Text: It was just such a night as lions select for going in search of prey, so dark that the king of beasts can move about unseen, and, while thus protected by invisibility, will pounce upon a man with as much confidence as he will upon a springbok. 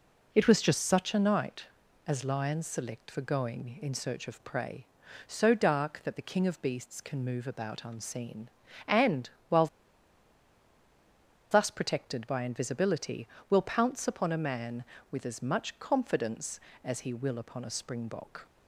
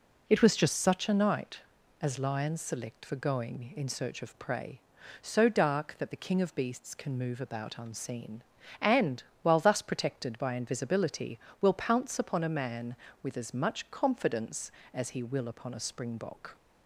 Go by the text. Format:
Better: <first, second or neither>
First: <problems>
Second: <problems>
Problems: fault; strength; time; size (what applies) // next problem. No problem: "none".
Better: second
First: pauses between "while" and "thus"; strong; at 9.6 s; 1.8 s long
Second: none